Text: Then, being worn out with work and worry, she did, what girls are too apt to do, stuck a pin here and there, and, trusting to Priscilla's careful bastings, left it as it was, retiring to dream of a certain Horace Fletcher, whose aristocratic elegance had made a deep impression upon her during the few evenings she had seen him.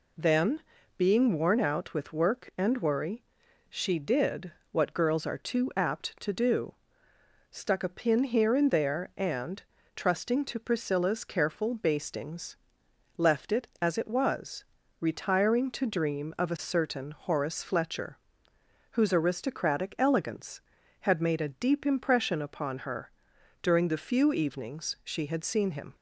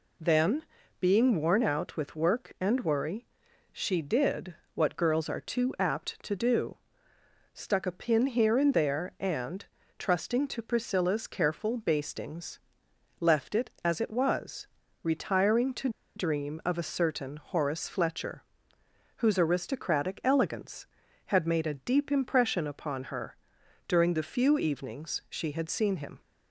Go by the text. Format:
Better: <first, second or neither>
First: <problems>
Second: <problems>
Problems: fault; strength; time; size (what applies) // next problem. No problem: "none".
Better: first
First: pauses between "her" and "during"; noticeable; at 23.0 s; 0.52 s long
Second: pauses between "to" and "dream"; slight; at 15.8 s; 0.27 s long // pauses between "her" and "during"; noticeable; at 23.3 s; 0.52 s long